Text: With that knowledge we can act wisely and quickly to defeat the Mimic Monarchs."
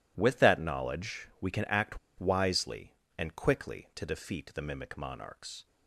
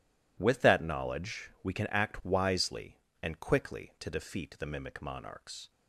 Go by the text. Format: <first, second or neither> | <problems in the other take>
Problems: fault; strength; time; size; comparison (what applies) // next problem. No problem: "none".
second | pauses between "act" and "wisely"; slight; at 1.9 s; 0.20 s long